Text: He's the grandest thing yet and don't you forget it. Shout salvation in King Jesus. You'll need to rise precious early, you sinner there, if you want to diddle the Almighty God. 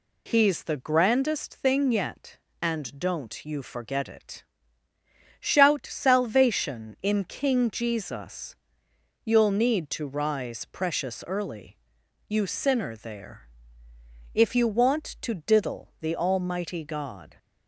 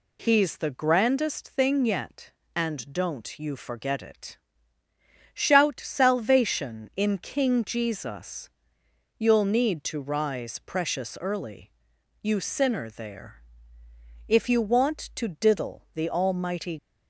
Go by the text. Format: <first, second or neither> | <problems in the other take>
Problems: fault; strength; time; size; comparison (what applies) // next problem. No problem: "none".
first | stops before "God"; at 16.7 s